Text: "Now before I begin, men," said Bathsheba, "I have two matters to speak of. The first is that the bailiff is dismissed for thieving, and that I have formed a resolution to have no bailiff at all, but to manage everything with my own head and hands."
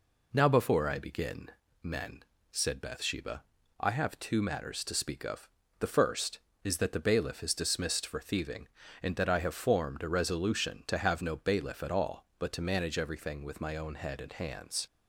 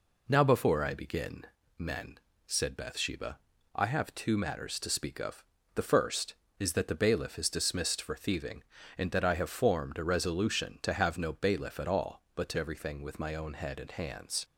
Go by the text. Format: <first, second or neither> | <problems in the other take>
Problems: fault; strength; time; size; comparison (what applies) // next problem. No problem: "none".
first | skips "manage"; at 12.5 s